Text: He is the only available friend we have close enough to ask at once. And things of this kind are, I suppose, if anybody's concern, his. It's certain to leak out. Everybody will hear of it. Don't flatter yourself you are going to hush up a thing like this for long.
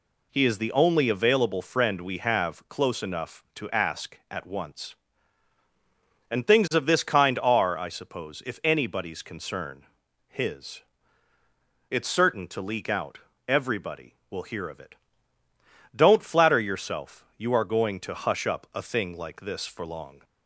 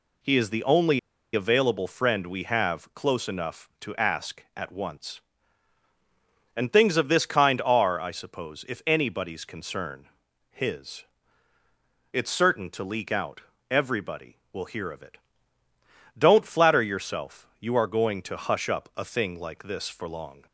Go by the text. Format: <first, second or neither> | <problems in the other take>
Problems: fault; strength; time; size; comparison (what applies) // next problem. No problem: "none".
first | pauses between "only" and "available"; slight; at 0.9 s; 0.34 s long